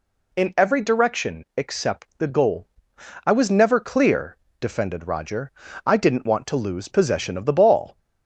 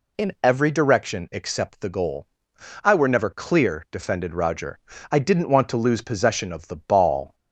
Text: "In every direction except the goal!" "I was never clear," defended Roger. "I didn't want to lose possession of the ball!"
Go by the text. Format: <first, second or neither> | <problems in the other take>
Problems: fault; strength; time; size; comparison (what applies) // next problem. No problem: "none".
first | says "were" for "was"; at 2.9 s